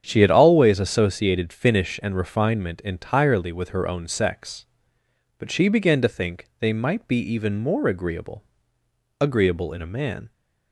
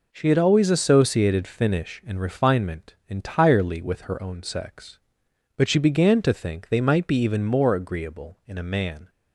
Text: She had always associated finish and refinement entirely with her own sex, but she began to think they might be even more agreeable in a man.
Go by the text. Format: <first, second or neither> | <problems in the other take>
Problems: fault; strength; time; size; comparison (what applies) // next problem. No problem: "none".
second | starts louder than the rest; strong; until 1.0 s; 8 dB // says "agreeable" twice; at 9.2 s